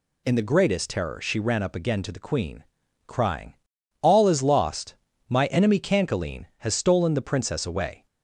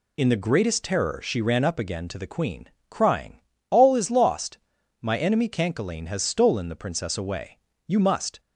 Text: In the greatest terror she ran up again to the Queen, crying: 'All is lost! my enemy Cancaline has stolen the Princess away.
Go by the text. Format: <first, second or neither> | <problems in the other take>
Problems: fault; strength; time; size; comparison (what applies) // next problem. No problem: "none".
first | goes on to say "You must"; from 7.8 s on; 0.52 s long